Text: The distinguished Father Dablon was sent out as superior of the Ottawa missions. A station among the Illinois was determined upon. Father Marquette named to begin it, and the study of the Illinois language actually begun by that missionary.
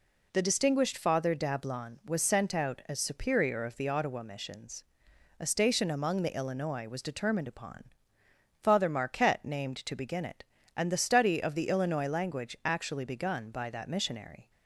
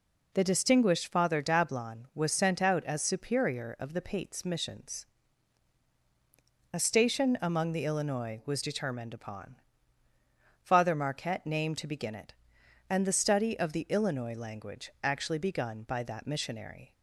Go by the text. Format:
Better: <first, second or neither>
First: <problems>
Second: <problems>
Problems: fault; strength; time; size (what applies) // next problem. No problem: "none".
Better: first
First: none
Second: says "Pates" for "Ottawa"; at 4.0 s